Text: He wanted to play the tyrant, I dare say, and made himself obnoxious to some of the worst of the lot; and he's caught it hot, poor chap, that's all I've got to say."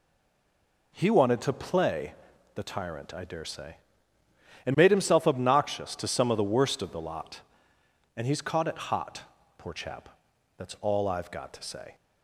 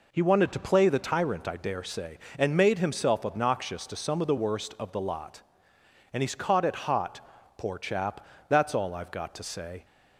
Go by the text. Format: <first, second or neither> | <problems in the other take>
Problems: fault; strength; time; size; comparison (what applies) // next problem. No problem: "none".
second | stays silent before the first word; slight; until 0.9 s; 0.9 s long // pauses between "play" and "the"; at 2.1 s; 0.40 s long